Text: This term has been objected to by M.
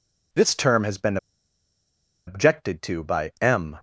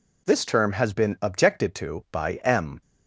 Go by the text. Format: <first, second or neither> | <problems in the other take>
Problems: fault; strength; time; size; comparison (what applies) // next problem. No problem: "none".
second | pauses between "been" and "objected"; at 1.1 s; 1.1 s long